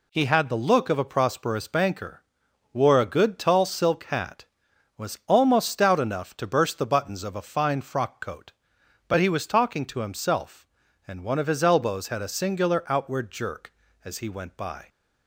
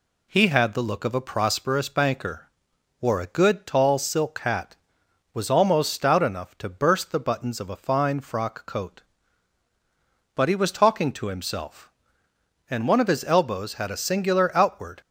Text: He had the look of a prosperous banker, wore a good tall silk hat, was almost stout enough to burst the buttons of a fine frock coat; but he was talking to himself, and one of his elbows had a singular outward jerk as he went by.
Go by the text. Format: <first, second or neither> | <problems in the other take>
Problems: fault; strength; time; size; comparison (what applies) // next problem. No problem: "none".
first | stops before "jerk as he went by"; at 15.0 s